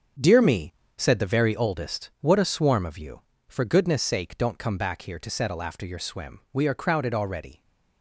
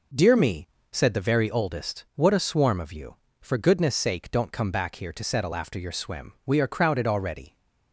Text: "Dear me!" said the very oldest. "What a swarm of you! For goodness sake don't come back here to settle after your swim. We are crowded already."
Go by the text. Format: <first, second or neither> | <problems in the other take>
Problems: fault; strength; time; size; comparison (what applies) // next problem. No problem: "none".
second | gets quieter; strong; throughout; 8 dB